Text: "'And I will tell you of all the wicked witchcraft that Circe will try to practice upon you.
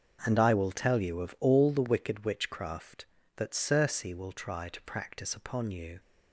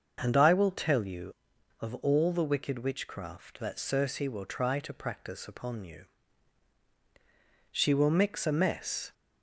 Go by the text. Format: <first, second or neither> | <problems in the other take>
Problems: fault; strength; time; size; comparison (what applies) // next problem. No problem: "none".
first | starts louder than the rest; until 1.2 s; 6.5 dB; also in the first // goes on to say "She will mix a mess"; from 7.7 s on; 1.4 s long